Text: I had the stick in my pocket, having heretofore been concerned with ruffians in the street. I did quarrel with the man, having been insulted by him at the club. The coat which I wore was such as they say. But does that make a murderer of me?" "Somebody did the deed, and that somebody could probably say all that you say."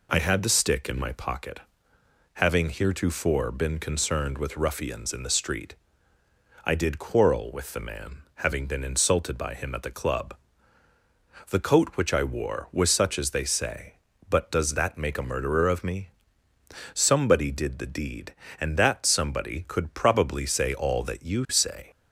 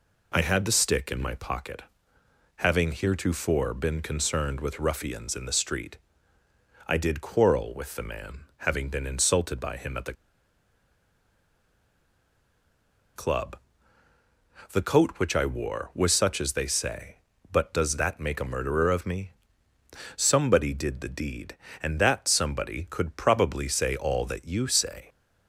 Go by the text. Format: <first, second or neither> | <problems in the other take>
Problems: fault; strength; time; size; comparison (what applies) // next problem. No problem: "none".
first | pauses between "the" and "club"; strong; at 10.1 s; 3.0 s long